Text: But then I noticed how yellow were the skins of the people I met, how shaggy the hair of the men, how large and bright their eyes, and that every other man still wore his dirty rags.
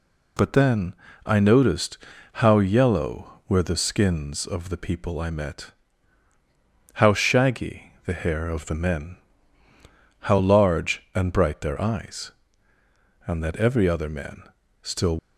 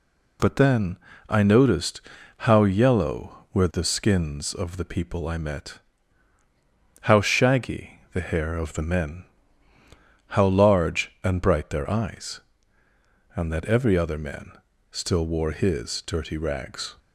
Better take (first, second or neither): second